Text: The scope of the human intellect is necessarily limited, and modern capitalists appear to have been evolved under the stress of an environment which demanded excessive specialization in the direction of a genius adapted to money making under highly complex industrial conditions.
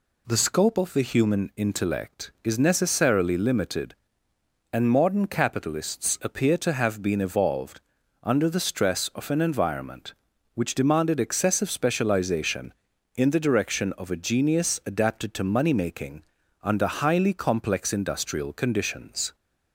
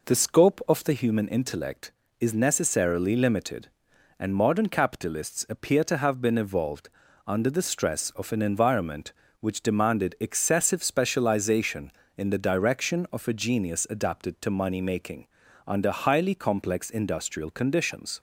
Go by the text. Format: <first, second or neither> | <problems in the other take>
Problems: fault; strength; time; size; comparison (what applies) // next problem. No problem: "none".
first | starts louder than the rest; noticeable; until 1.1 s; 4.5 dB // pauses between "evolved" and "under"; slight; at 6.8 s; 0.36 s long; also in the first // pauses between "making" and "under"; at 15.2 s; 0.40 s long; also in the first